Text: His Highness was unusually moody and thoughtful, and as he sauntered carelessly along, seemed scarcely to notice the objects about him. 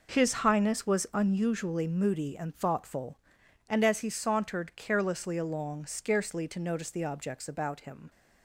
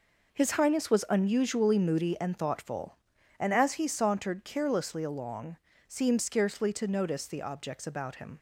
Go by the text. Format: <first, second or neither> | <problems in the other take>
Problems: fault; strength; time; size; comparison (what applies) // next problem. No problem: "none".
second | skips "seemed"; at 5.8 s